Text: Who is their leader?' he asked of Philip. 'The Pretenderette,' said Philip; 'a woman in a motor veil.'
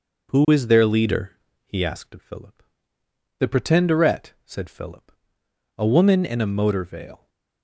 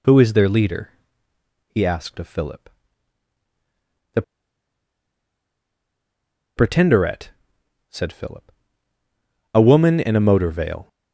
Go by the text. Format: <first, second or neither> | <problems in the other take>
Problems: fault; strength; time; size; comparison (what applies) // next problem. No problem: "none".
first | pauses between "The" and "Pretenderette"; strong; at 4.2 s; 2.3 s long